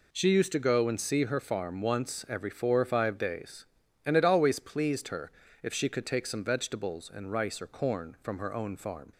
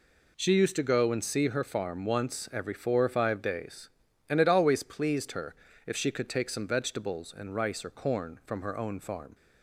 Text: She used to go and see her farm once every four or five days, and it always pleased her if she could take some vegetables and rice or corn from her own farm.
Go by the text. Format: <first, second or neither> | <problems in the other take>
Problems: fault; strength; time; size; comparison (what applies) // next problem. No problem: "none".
neither | pauses between "her" and "if"; slight; the same in both